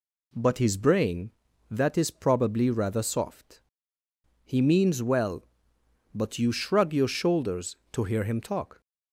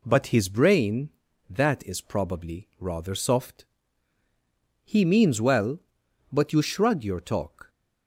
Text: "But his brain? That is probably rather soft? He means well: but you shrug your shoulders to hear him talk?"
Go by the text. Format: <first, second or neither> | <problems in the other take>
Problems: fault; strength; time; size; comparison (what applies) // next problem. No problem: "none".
first | skips "shoulders to hear him"; at 7.1 s